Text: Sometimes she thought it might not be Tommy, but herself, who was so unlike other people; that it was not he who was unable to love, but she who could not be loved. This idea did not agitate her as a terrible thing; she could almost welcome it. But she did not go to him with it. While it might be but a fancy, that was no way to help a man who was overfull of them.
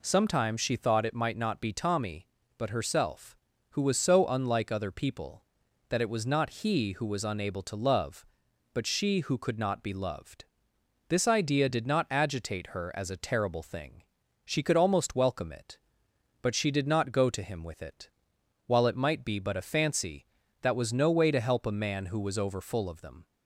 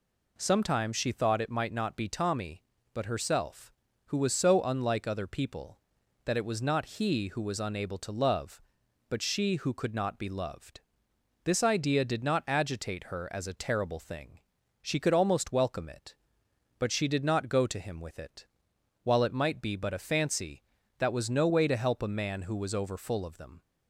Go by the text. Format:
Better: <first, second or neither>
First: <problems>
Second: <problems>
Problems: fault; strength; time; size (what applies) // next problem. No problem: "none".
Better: neither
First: none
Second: none